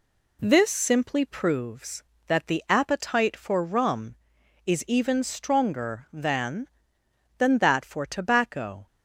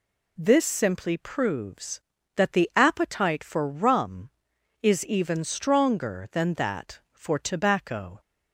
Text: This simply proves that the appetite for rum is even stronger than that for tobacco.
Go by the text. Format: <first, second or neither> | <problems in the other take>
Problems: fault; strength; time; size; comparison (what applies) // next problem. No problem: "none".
second | says "than" twice; at 7.3 s